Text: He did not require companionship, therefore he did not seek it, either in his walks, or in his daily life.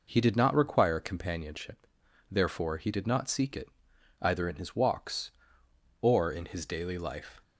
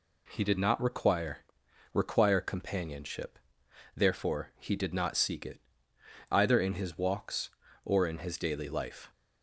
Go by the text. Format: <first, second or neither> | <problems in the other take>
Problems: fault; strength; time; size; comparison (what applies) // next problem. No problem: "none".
first | says "require" twice; at 1.9 s